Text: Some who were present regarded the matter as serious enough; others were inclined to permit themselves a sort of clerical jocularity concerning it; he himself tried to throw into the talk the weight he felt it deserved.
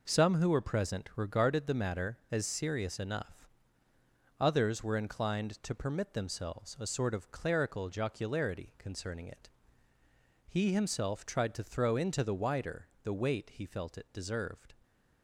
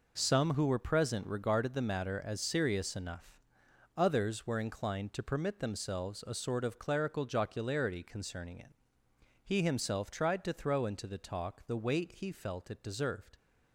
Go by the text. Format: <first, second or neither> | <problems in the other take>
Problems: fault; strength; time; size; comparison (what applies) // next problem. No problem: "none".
second | says "wider" for "talk"; at 12.3 s